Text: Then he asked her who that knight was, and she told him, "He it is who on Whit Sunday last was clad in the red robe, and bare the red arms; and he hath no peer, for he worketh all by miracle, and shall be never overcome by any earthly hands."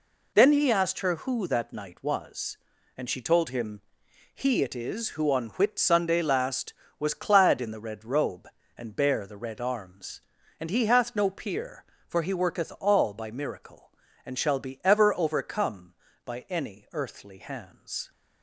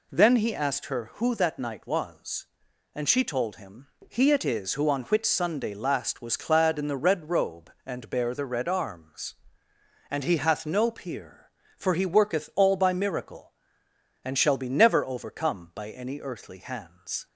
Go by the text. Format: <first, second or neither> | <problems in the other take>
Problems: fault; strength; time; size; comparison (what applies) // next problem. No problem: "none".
second | says "ever" for "never"; at 14.8 s